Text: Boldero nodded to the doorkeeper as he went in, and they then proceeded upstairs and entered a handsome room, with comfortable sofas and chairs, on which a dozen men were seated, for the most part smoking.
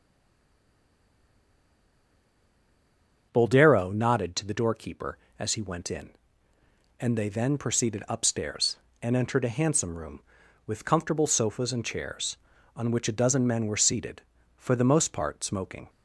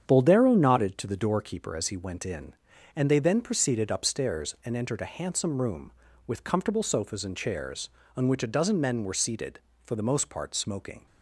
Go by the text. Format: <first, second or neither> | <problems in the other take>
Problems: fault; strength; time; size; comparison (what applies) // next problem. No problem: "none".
second | stays silent before the first word; strong; until 3.3 s; 3.3 s long // starts louder than the rest; until 4.3 s; 7 dB; strong in the second